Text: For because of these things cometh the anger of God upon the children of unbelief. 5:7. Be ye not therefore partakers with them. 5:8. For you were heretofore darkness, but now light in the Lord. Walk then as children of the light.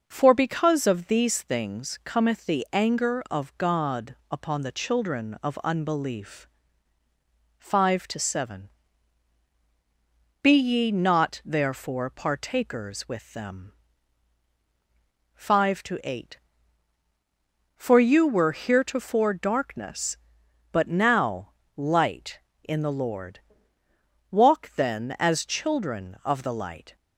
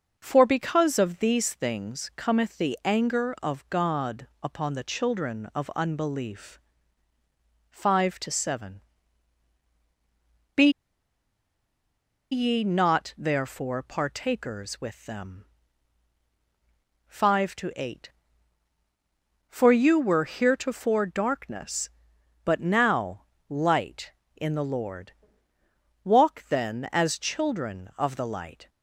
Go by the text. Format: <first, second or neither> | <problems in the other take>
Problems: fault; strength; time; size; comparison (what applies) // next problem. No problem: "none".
first | pauses between "Be" and "ye"; strong; at 10.6 s; 1.6 s long // pauses between "now" and "light"; slight; at 23.2 s; 0.24 s long; slight in the first